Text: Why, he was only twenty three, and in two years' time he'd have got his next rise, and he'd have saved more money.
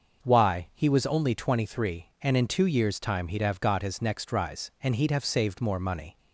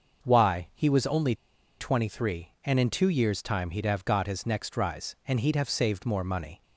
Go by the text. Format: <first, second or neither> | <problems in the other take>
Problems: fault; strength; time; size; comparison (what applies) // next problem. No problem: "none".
first | starts louder than the rest; until 1.3 s; 6 dB; noticeable in the first // pauses between "only" and "twenty"; at 1.3 s; 0.44 s long